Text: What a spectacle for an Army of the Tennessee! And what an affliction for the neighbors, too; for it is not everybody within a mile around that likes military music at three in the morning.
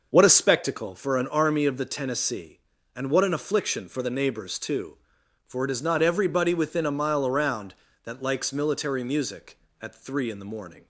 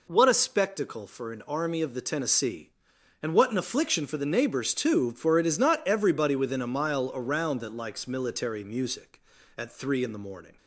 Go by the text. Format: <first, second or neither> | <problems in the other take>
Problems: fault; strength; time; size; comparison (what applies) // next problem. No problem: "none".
neither | none